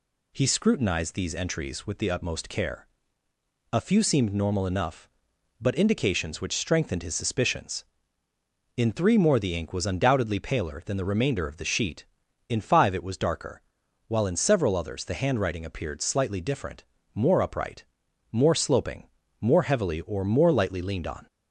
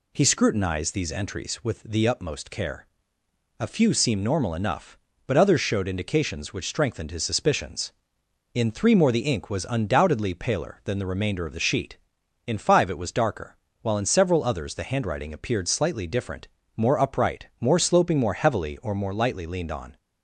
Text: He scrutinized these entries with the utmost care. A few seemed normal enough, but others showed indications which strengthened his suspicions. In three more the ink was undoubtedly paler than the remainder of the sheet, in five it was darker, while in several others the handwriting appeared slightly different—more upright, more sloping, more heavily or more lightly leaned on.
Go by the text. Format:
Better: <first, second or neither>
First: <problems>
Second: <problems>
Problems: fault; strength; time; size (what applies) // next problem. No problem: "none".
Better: second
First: skips "others showed"; at 5.7 s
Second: none